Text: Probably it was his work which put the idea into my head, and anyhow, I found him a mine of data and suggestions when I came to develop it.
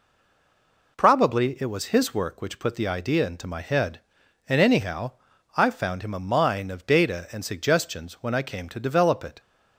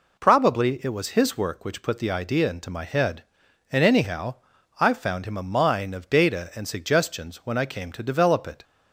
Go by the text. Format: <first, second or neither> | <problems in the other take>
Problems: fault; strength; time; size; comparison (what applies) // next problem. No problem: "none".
second | stays silent before the first word; slight; until 0.9 s; 0.9 s long